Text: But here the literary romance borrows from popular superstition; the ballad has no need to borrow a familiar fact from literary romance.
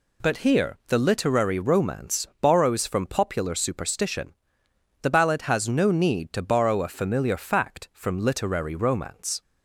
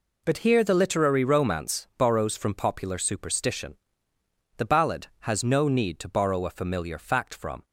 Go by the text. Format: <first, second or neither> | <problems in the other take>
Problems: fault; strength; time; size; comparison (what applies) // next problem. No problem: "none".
first | stops before "literary romance"; at 7.6 s